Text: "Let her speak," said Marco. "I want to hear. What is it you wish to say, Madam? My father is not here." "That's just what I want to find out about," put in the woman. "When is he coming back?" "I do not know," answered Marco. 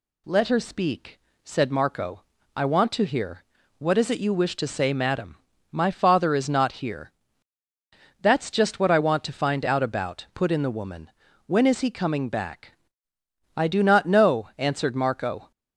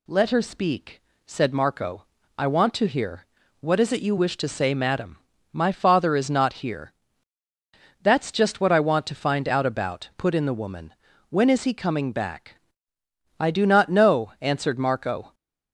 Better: neither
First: none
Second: none

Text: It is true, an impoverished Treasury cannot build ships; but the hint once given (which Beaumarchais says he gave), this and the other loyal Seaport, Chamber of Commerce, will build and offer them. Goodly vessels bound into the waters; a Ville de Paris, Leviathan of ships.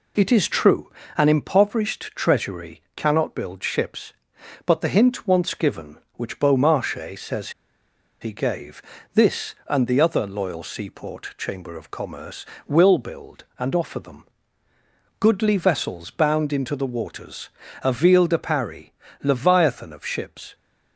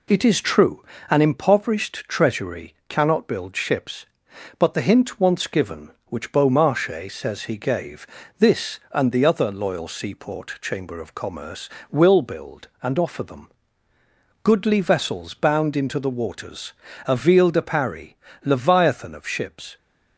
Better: second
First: pauses between "Treasury" and "cannot"; slight; at 2.8 s; 0.16 s long // pauses between "says" and "he"; noticeable; at 7.5 s; 0.70 s long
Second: pauses between "Treasury" and "cannot"; slight; at 2.7 s; 0.16 s long

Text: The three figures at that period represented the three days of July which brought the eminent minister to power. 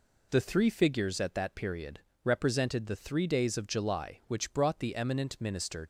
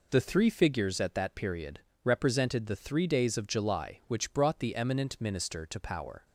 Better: second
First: pauses between "period" and "represented"; slight; at 2.0 s; 0.22 s long // stops before "to power"; at 5.8 s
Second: pauses between "period" and "represented"; slight; at 1.8 s; 0.22 s long

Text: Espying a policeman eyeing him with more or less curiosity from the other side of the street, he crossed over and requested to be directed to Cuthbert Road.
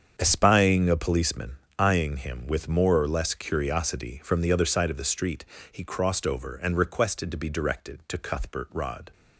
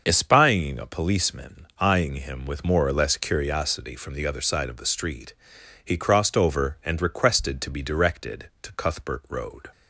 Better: second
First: starts louder than the rest; strong; until 1.2 s; 7.5 dB // pauses between "policeman" and "eyeing"; slight; at 1.5 s; 0.20 s long // says "Rod" for "Road"; at 8.7 s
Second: starts louder than the rest; until 1.0 s; 6 dB

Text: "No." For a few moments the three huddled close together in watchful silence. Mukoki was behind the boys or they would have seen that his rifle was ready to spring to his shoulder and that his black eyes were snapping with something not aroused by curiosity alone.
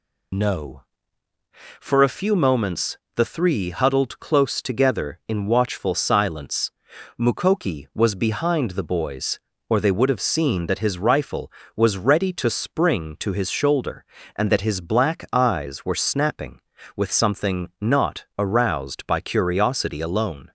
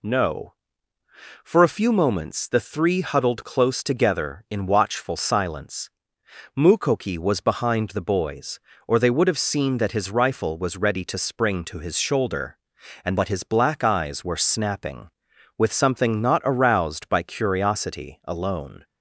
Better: second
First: loses the start of "No"; at 0.3 s; 50 ms // pauses between "moments" and "the"; slight; at 2.9 s; 0.18 s long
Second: none

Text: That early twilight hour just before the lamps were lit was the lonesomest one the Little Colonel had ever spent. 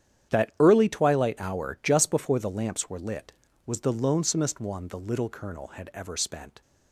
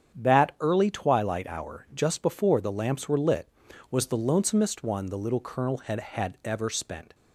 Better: first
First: starts louder than the rest; strong; until 1.3 s; 9.5 dB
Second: starts louder than the rest; strong; until 1.2 s; 8.5 dB // says "had" twice; at 6.0 s

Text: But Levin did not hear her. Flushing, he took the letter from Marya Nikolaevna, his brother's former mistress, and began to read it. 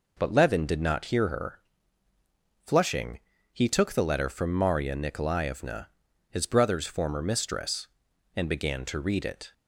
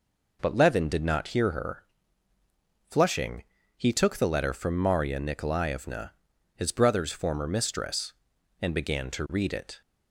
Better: neither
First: none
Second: none

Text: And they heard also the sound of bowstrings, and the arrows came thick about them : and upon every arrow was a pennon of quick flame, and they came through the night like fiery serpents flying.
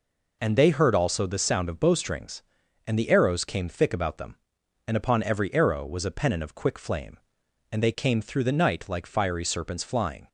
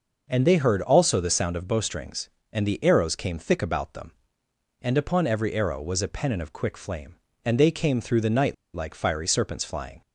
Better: first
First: none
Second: pauses between "night" and "like"; slight; at 8.5 s; 0.20 s long

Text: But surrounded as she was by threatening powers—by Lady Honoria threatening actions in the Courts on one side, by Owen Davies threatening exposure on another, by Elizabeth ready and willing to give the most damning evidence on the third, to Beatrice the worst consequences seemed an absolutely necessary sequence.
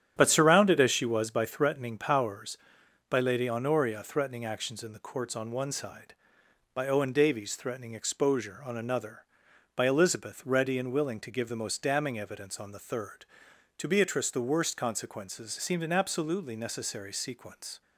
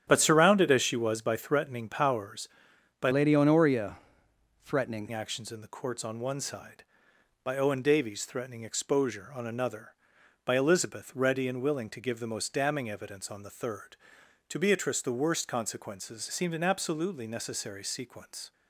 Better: first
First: starts louder than the rest; strong; until 1.1 s; 10 dB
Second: starts louder than the rest; strong; until 1.0 s; 9.5 dB // changes voice from "Lady" to "threatening"; from 3.1 to 5.0 s; 1.9 s long // pauses between "Honoria" and "threatening"; noticeable; at 3.9 s; 0.66 s long

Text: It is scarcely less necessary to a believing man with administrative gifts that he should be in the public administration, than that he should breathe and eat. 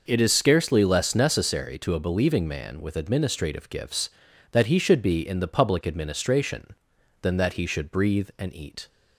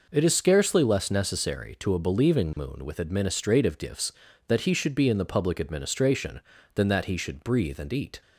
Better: first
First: none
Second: says "moon" for "man"; at 2.5 s

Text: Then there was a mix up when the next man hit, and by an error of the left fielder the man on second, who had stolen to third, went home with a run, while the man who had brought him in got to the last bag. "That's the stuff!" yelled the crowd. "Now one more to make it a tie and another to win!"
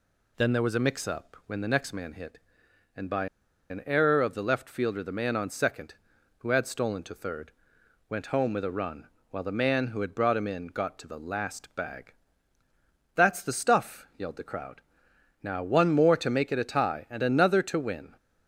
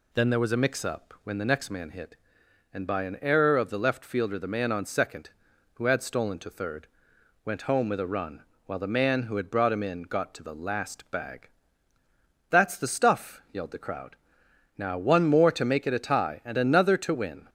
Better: second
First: pauses between "by" and "an"; at 3.2 s; 0.43 s long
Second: none

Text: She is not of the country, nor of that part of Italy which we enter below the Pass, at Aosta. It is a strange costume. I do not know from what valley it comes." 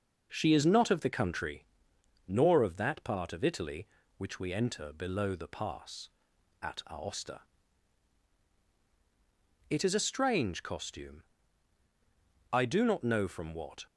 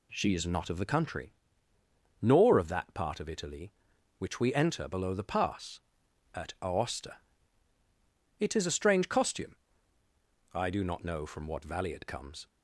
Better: second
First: stops before "valley it comes"; at 13.8 s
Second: none

